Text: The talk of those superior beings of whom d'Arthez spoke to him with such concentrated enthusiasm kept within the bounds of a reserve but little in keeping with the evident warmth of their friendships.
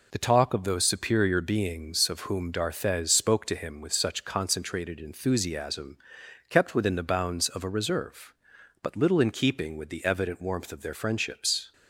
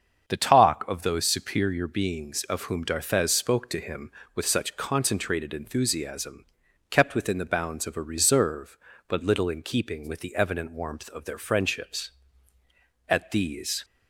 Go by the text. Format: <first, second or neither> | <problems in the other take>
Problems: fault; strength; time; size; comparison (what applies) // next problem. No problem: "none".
first | starts louder than the rest; strong; until 1.3 s; 7.5 dB // pauses between "enthusiasm" and "kept"; at 6.4 s; 0.42 s long; noticeable in the first // goes on to say "At these"; noticeable; from 13.0 s on; 0.78 s long